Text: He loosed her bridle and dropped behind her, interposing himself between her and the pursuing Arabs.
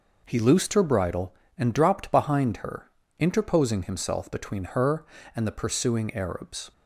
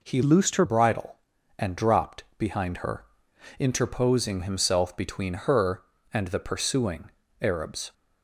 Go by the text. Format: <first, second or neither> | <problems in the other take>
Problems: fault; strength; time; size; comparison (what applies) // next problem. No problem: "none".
first | changes voice from "loosed" to "her"; from 0.2 to 0.6 s; 0.4 s long // pauses between "dropped" and "behind"; slight; at 2.2 s; 0.16 s long // pauses between "pursuing" and "Arabs"; slight; at 7.1 s; 0.30 s long